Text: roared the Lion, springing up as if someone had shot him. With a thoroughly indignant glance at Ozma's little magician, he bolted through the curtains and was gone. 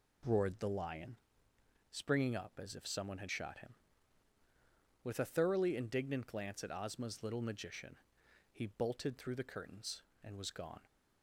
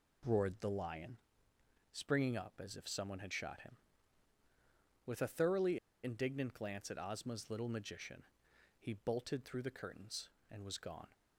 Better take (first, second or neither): first